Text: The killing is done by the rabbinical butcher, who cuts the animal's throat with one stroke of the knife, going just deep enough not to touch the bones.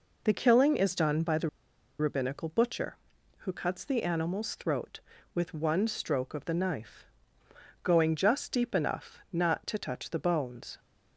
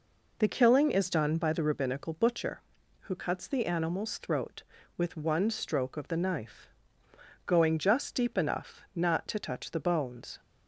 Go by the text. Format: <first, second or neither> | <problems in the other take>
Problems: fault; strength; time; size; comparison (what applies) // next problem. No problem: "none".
second | pauses between "the" and "rabbinical"; noticeable; at 1.4 s; 0.50 s long